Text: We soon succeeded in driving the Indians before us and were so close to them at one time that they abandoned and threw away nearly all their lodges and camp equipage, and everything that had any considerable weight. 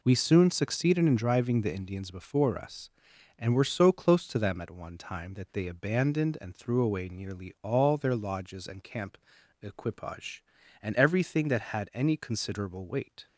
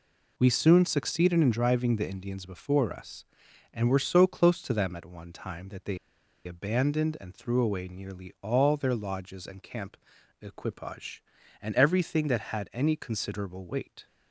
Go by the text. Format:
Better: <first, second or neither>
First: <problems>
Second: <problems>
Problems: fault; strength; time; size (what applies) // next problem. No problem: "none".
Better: first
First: pauses between "camp" and "equipage"; noticeable; at 9.1 s; 0.46 s long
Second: pauses between "they" and "abandoned"; noticeable; at 5.9 s; 0.48 s long // pauses between "camp" and "equipage"; noticeable; at 9.9 s; 0.46 s long